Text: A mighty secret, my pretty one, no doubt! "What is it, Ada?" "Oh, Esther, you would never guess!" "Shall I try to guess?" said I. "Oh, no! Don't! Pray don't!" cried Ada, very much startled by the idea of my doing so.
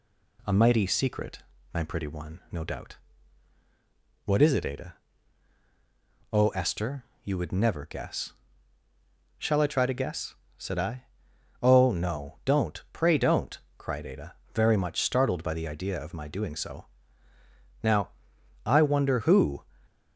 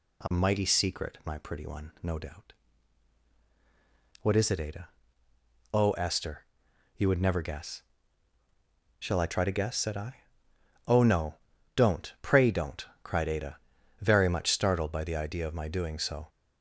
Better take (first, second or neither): second